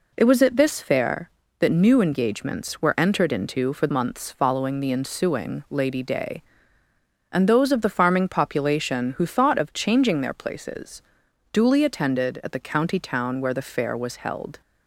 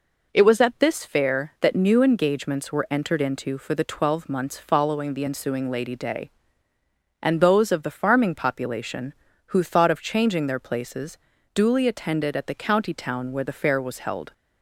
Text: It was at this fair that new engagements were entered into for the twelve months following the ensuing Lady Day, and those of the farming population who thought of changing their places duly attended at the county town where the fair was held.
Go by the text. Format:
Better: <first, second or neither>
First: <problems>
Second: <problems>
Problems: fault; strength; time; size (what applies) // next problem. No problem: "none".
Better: second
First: skips "the twelve"; at 3.8 s // pauses between "places" and "duly"; noticeable; at 11.0 s; 0.50 s long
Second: pauses between "places" and "duly"; at 11.1 s; 0.38 s long